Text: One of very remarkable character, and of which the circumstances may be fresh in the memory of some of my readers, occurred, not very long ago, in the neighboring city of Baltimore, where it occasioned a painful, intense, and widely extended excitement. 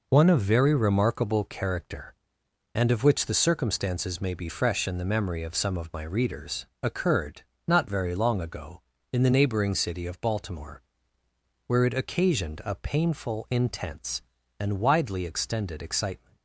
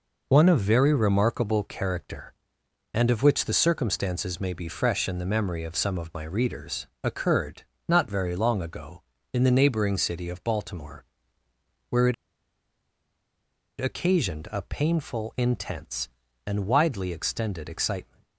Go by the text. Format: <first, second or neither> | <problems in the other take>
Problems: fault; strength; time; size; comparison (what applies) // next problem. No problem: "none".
first | pauses between "it" and "occasioned"; strong; at 12.1 s; 1.6 s long